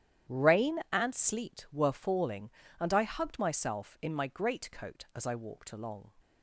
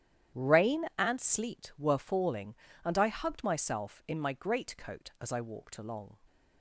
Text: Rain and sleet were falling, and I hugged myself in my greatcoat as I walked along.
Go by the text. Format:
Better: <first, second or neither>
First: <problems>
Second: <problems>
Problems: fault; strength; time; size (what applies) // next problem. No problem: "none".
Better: neither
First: starts louder than the rest; strong; until 1.4 s; 10.5 dB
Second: starts louder than the rest; strong; until 1.4 s; 10.5 dB